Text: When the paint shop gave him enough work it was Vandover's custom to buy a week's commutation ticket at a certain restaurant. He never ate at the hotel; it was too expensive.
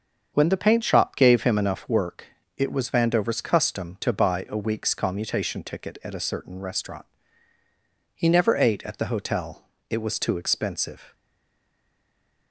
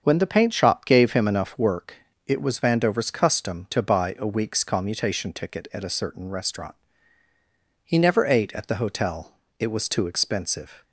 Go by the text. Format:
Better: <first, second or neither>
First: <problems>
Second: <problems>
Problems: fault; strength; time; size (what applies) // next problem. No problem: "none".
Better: second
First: starts louder than the rest; until 1.3 s; 7 dB // pauses between "work" and "it"; slight; at 2.2 s; 0.30 s long // stays silent after the last word; noticeable; from 11.1 s on; 1.4 s long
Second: starts louder than the rest; until 1.0 s; 7 dB // pauses between "work" and "it"; slight; at 1.9 s; 0.30 s long